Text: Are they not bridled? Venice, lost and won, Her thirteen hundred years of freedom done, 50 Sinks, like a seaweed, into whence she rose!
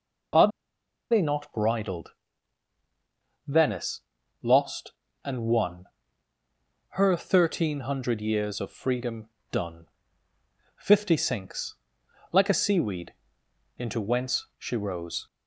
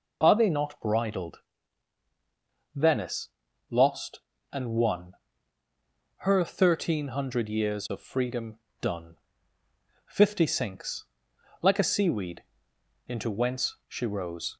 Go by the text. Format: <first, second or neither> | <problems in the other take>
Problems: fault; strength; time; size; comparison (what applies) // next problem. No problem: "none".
second | pauses between "Are" and "they"; noticeable; at 0.4 s; 0.62 s long // pauses between "freedom" and "done"; slight; at 9.2 s; 0.22 s long; slight in the second